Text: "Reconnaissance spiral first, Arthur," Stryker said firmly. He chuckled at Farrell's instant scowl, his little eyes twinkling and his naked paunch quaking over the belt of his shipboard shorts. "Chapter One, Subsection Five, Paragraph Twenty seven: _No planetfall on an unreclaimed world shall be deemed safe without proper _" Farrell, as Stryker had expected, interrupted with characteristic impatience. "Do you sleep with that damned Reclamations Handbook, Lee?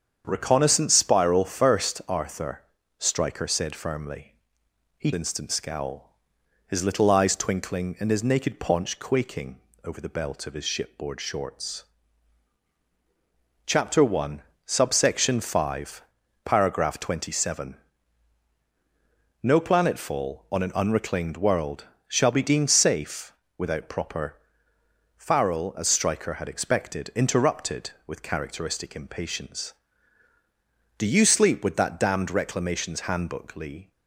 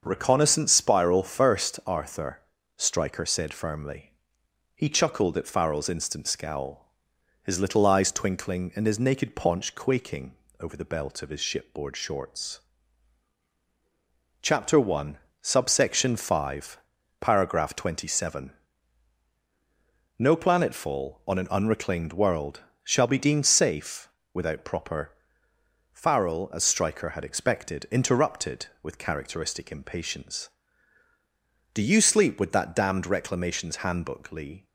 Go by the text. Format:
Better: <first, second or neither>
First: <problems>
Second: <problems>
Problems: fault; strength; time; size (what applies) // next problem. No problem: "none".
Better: second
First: starts louder than the rest; strong; until 1.2 s; 7.5 dB // skips "chuckled at Farrell's"; at 5.1 s // pauses between "quaking" and "over"; slight; at 9.5 s; 0.24 s long // pauses between "world" and "shall"; slight; at 21.8 s; 0.22 s long // pauses between "safe" and "without"; slight; at 23.3 s; 0.24 s long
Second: starts louder than the rest; until 1.0 s; 6.5 dB // pauses between "quaking" and "over"; slight; at 10.3 s; 0.24 s long // pauses between "world" and "shall"; slight; at 22.6 s; 0.22 s long // pauses between "safe" and "without"; slight; at 24.0 s; 0.24 s long